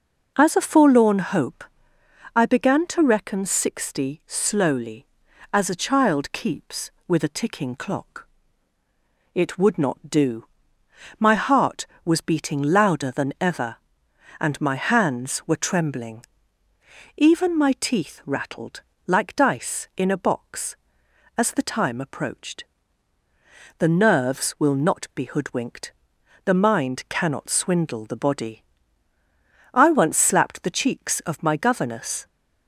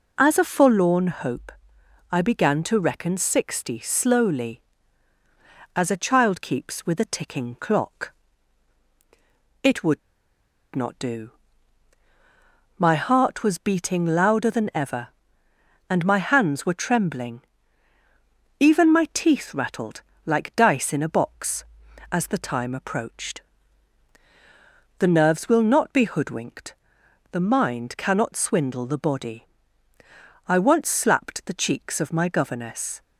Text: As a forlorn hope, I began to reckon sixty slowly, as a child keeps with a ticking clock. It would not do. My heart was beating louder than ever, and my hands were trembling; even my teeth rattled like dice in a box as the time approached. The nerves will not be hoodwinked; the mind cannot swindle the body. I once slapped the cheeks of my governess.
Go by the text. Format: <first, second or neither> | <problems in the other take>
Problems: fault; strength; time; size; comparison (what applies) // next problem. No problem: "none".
first | pauses between "would" and "not"; noticeable; at 10.0 s; 0.74 s long // pauses between "rattled" and "like"; slight; at 20.0 s; 0.24 s long; slight in the first